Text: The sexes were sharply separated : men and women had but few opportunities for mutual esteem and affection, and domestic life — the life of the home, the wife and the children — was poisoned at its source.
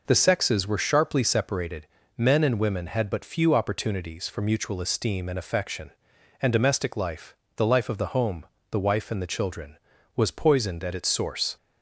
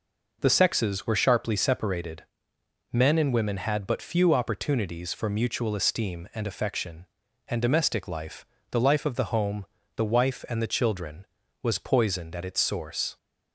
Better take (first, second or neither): neither